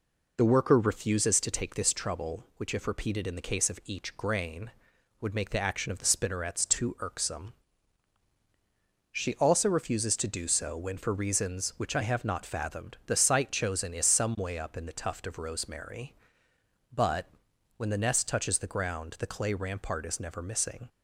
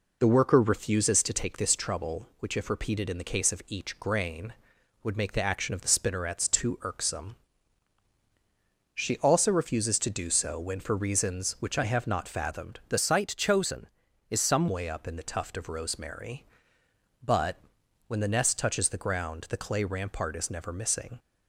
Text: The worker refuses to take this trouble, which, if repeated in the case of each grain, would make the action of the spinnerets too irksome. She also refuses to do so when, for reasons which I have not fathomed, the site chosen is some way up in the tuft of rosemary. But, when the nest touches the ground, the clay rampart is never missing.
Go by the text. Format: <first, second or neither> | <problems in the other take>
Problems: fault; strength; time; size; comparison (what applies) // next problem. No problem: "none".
first | changes voice from "site" to "some"; from 12.9 to 14.6 s; 1.7 s long